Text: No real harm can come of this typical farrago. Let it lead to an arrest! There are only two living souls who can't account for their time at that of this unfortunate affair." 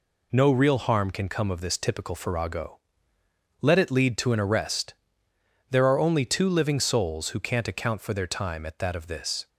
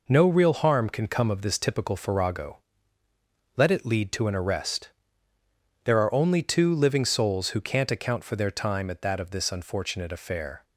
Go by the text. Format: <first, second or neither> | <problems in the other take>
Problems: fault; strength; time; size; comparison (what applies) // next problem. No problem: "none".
second | stops before "unfortunate affair"; at 9.4 s